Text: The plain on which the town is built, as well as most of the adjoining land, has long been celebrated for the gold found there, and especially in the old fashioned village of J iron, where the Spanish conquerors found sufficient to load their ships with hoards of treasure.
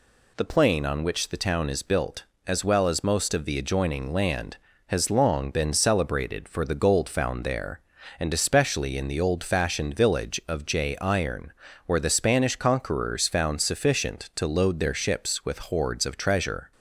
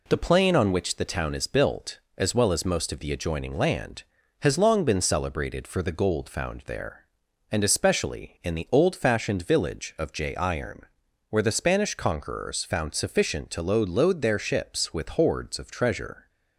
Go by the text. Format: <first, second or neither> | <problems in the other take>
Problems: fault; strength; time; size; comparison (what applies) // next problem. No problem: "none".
first | says "load" twice; at 13.8 s